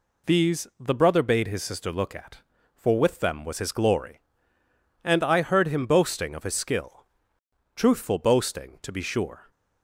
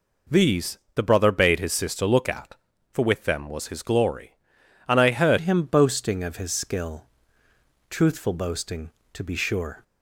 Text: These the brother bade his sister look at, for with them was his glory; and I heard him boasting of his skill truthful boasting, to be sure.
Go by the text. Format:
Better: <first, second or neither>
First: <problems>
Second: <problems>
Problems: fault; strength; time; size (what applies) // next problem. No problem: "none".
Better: first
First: pauses between "skill" and "truthful"; noticeable; at 7.0 s; 0.72 s long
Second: pauses between "These" and "the"; slight; at 0.7 s; 0.16 s long // changes voice at "him"; from 5.4 s on; 4.4 s long // pauses between "skill" and "truthful"; noticeable; at 7.0 s; 0.82 s long